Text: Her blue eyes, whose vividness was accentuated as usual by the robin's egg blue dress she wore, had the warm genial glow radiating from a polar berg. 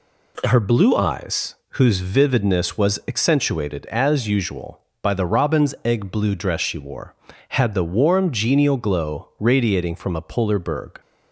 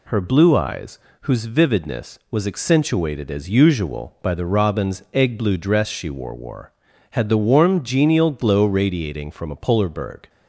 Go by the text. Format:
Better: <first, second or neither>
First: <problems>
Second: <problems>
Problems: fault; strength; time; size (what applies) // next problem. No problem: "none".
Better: first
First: none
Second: says "wore" twice; at 6.3 s